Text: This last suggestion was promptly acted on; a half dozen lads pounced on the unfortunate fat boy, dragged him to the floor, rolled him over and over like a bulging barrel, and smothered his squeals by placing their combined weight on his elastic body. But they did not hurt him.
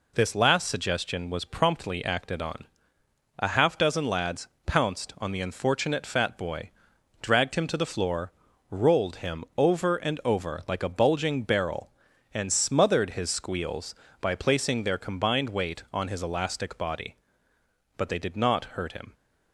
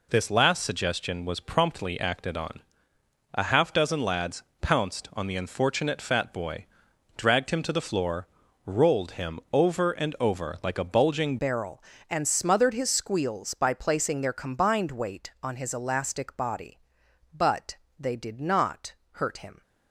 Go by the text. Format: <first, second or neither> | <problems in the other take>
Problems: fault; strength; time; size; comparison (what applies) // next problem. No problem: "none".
first | pauses between "lads" and "pounced"; slight; at 4.4 s; 0.22 s long; slight in the first // changes voice at "barrel"; from 11.3 s on; 8.3 s long // pauses between "But" and "they"; slight; at 17.7 s; 0.24 s long // pauses between "not" and "hurt"; slight; at 18.9 s; 0.18 s long